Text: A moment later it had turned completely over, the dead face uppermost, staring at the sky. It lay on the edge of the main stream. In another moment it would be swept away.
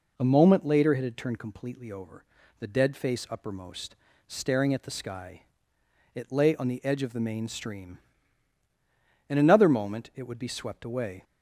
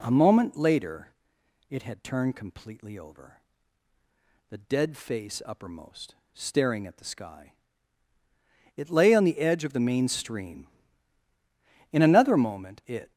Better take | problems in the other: first | pauses between "later" and "it"; noticeable; at 1.0 s; 0.60 s long // stops before "would be swept away"; at 13.1 s

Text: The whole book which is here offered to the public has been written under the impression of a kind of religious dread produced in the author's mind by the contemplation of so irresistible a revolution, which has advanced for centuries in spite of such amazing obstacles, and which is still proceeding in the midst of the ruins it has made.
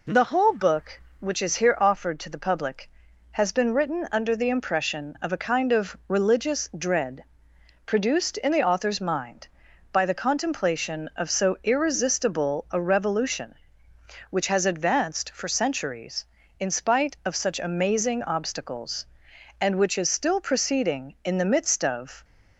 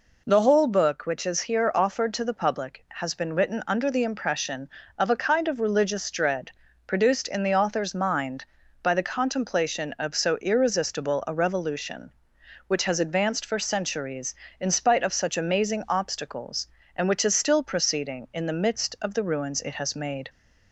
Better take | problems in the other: second | pauses between "dread" and "produced"; noticeable; at 7.2 s; 0.58 s long; slight in the second // stops before "the ruins it has made"; at 22.2 s

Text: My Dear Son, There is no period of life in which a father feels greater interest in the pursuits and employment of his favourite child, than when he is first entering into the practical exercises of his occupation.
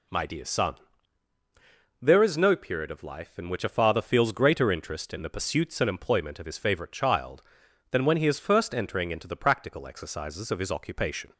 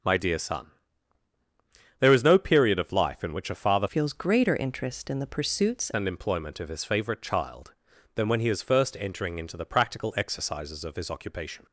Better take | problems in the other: first | changes voice from "feels" to "pursuits"; from 3.8 to 5.9 s; 2.1 s long

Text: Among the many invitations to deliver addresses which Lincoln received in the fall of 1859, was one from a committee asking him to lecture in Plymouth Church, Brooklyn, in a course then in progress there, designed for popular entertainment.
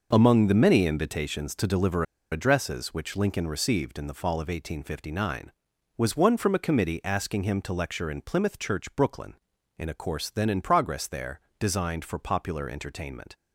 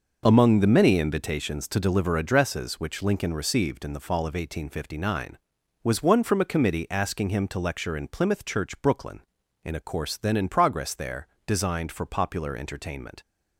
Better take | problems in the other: second | pauses between "deliver" and "addresses"; slight; at 2.0 s; 0.28 s long

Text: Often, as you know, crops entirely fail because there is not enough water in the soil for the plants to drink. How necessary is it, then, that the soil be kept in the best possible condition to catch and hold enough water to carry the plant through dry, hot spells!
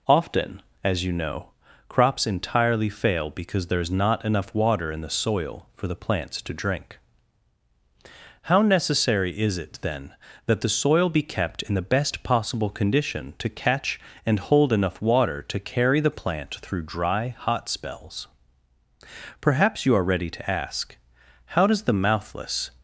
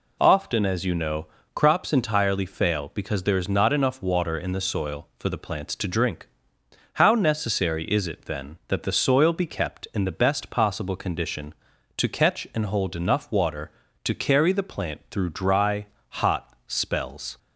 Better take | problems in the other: second | goes on to say "Perhaps you are ready to ask How does the mouthless"; strong; from 19.3 s on; 3.3 s long

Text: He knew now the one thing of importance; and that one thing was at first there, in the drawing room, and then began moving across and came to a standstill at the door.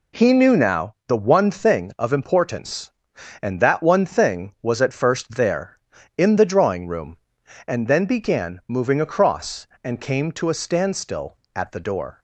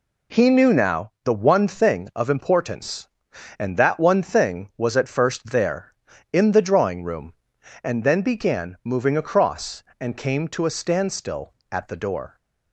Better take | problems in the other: neither | none

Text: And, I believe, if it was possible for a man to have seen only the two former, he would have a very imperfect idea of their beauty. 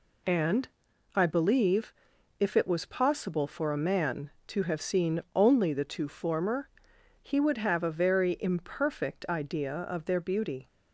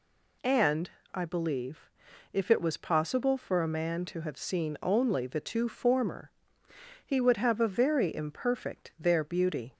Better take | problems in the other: first | skips "idea of"; at 8.9 s

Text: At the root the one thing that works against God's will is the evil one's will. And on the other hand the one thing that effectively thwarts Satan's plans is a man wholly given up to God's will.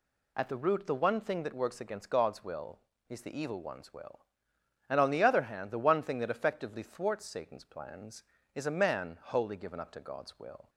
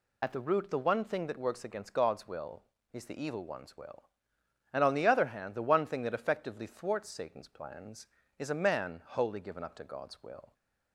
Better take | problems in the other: first | loses the start of "At"; at 0.2 s; 35 ms

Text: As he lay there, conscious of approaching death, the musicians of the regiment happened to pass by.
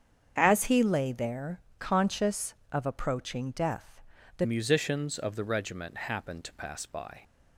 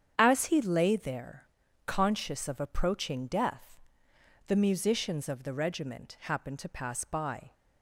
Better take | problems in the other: second | starts louder than the rest; strong; until 1.3 s; 7.5 dB; strong in the second // changes voice at "musicians"; from 4.4 s on; 2.8 s long

